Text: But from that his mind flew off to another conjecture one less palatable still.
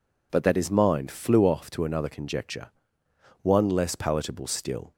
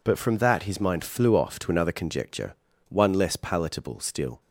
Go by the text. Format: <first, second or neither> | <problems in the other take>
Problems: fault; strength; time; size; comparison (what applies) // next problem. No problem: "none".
second | skips "from"; at 0.4 s // pauses between "conjecture" and "one"; noticeable; at 2.7 s; 0.72 s long; slight in the second